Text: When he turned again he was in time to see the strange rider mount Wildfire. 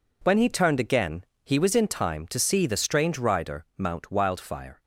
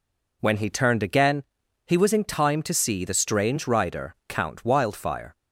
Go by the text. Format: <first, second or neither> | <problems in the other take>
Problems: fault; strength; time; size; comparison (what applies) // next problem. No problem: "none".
first | pauses between "again" and "he"; at 1.4 s; 0.42 s long; slight in the first // says "count" for "mount"; at 4.2 s